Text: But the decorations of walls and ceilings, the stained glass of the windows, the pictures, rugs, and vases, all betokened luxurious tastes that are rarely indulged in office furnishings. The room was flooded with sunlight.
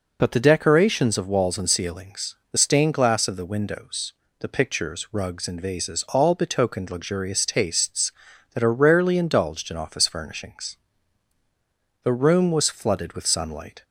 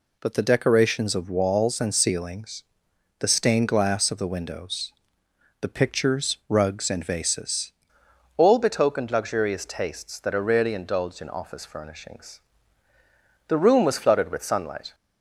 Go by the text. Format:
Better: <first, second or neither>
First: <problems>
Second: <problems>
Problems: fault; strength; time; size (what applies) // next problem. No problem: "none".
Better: first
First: none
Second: changes voice at "all"; from 8.3 s on; 6.6 s long